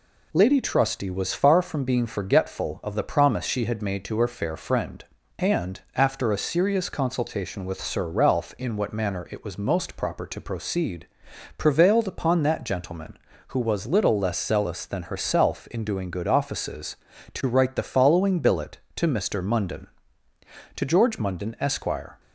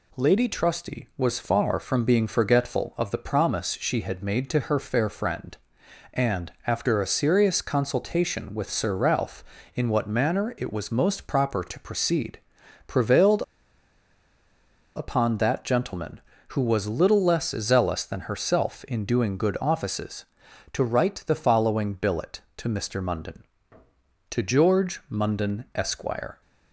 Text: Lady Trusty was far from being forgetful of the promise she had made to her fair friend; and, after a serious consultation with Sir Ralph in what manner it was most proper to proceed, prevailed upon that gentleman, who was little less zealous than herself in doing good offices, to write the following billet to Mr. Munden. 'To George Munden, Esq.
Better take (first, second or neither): first